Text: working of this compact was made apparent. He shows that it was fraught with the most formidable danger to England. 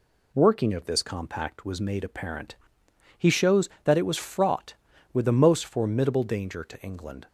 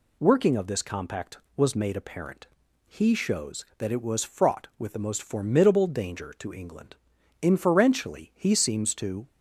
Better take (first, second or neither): first